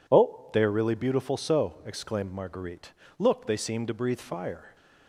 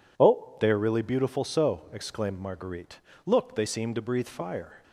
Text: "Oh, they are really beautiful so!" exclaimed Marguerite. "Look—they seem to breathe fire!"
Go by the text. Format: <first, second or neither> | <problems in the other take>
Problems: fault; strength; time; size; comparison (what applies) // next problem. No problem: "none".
neither | none